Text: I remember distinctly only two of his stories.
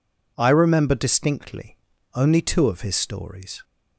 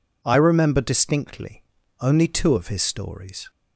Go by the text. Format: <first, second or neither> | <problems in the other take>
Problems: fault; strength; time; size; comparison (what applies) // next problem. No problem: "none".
neither | pauses between "distinctly" and "only"; slight; the same in both